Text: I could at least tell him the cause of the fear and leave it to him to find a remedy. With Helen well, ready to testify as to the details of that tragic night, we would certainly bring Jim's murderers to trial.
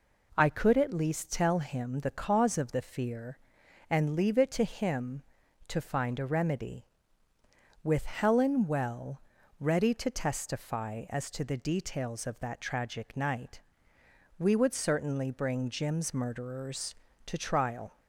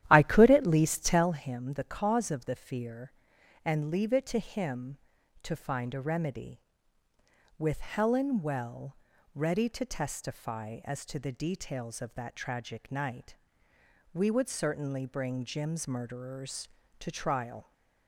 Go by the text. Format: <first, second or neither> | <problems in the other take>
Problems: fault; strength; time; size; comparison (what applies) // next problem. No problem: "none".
first | starts louder than the rest; strong; until 1.3 s; 12 dB